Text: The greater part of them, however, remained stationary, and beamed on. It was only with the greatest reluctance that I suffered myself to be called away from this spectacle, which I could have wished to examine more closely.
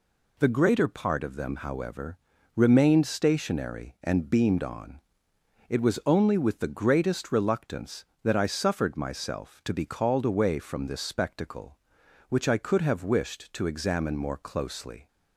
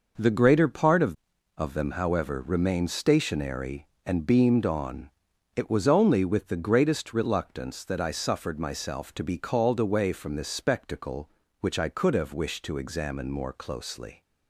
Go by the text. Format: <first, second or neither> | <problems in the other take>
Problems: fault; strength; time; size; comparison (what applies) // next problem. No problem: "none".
first | says "of" twice; at 1.5 s